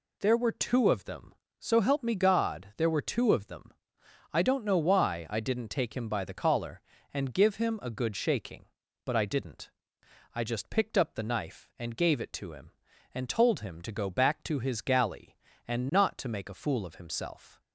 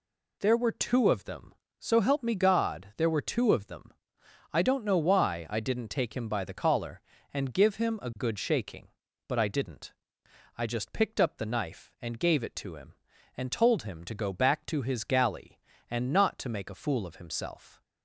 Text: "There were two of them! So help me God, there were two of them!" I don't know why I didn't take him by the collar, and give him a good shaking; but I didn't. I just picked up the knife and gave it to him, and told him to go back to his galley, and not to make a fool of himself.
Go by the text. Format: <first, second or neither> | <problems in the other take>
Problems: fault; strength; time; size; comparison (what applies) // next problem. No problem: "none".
neither | none